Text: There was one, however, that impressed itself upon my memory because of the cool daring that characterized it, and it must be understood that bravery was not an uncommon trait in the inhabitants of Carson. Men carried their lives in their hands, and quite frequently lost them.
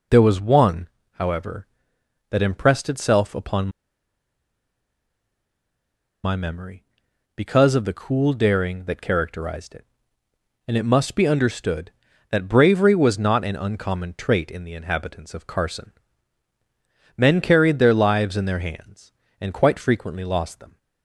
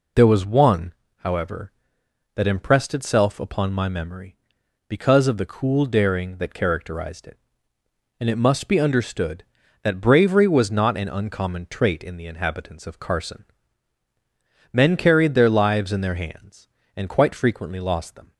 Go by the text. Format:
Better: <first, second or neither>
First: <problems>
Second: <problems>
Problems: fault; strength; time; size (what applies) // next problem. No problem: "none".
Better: second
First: pauses between "upon" and "my"; strong; at 3.6 s; 2.5 s long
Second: none